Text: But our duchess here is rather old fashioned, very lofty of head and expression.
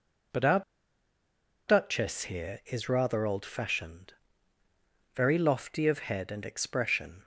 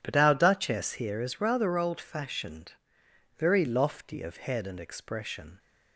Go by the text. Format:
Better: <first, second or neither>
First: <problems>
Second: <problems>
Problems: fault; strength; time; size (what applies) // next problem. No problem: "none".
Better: second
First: pauses between "our" and "duchess"; at 0.6 s; 1.0 s long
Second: none